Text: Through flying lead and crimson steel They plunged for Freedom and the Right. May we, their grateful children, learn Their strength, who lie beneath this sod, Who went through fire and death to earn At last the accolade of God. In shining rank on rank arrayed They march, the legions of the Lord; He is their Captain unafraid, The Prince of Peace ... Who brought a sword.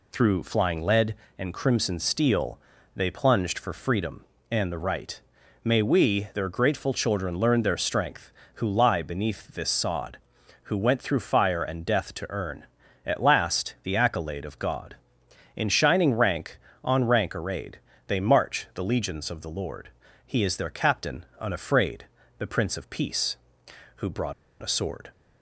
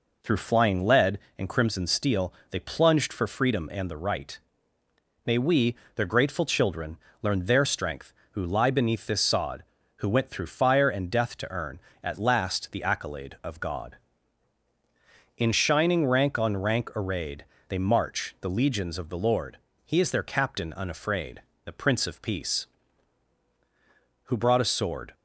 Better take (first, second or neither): second